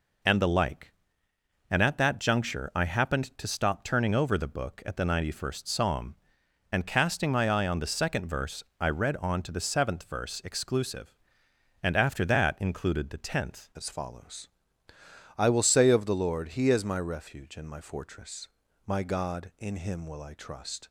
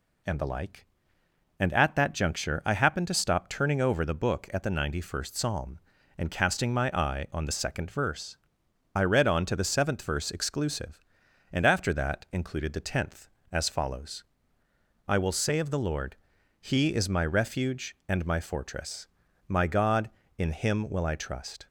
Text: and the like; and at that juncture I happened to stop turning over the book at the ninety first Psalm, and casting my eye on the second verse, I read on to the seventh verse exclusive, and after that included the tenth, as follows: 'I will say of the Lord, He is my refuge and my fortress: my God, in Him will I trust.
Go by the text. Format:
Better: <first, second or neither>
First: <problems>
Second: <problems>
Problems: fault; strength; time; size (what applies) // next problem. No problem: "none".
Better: second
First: changes voice at "as"; from 13.7 s on; 7.1 s long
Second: none